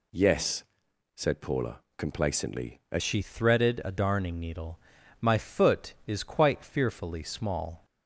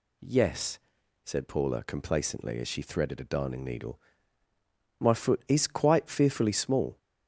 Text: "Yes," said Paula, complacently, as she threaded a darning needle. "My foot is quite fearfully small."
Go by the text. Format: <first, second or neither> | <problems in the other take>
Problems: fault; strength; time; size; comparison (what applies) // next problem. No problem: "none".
second | changes voice at "she"; from 3.0 s on; 4.8 s long